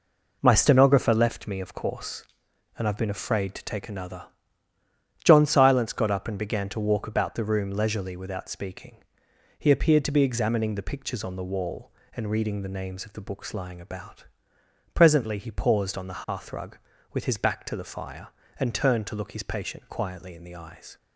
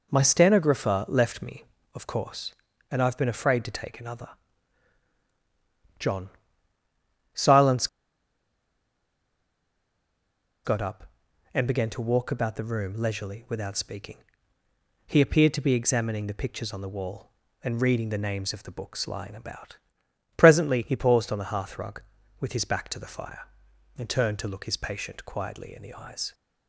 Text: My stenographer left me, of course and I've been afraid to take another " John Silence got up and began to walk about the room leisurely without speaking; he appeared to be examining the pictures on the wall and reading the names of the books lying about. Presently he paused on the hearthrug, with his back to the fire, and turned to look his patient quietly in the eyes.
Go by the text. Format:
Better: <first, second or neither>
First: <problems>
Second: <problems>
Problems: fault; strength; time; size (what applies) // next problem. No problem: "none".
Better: first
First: none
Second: pauses between "John" and "Silence"; at 6.3 s; 1.0 s long // pauses between "Silence" and "got"; strong; at 7.8 s; 2.7 s long